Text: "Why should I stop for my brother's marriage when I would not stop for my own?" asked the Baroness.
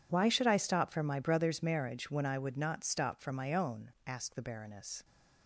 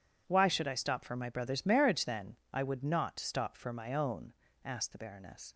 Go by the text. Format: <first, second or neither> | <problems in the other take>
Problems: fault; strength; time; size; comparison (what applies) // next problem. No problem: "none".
first | says "then" for "when"; at 2.0 s